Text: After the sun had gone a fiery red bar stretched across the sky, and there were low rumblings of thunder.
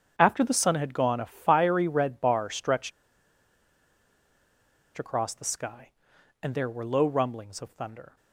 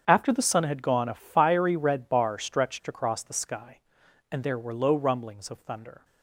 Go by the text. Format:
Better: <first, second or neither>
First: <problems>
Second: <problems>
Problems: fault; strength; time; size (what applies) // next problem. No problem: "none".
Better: second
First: starts louder than the rest; strong; until 1.1 s; 8 dB // pauses between "stretched" and "across"; strong; at 2.9 s; 2.0 s long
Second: starts louder than the rest; strong; until 1.0 s; 8 dB